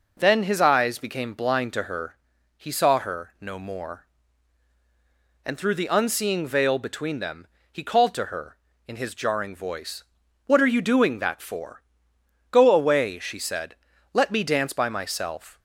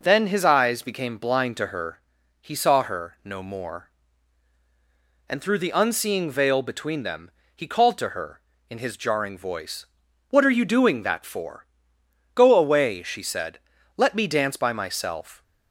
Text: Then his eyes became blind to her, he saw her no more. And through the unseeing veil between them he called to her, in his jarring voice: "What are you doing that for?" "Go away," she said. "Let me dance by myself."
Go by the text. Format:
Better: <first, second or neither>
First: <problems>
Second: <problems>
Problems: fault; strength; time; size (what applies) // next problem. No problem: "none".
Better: neither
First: pauses between "them" and "he"; slight; at 7.4 s; 0.26 s long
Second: pauses between "them" and "he"; slight; at 7.2 s; 0.26 s long